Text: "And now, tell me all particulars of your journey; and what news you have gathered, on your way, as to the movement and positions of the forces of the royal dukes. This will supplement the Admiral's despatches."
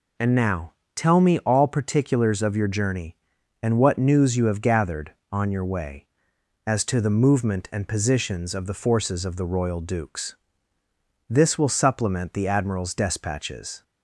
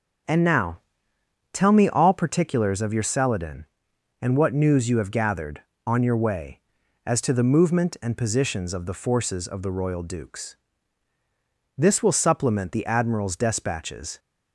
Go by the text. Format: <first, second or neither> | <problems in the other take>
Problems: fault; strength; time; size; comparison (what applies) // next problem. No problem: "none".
first | says "celadon" for "journey"; at 3.0 s